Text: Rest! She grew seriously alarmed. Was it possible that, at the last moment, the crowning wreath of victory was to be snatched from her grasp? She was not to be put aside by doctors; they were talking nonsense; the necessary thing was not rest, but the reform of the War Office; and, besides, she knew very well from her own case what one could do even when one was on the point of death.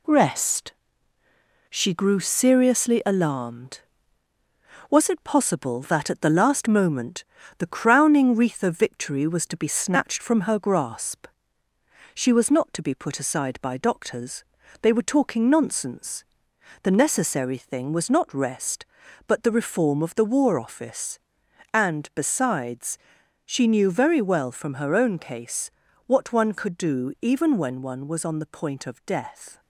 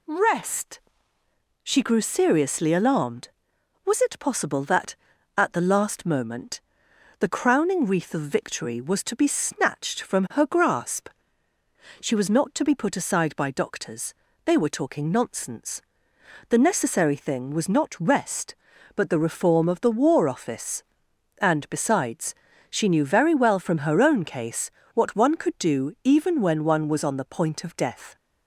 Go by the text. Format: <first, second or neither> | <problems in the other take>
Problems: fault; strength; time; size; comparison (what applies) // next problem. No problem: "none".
second | gets quieter; noticeable; throughout; 4.5 dB // pauses between "case" and "what"; slight; at 25.6 s; 0.36 s long; slight in the second